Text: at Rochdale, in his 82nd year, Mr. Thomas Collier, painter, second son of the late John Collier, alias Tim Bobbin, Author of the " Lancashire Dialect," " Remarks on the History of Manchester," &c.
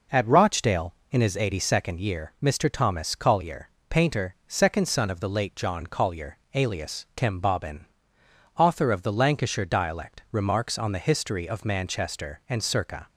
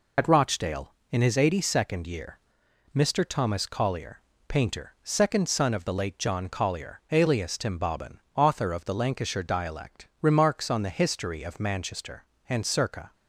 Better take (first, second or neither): first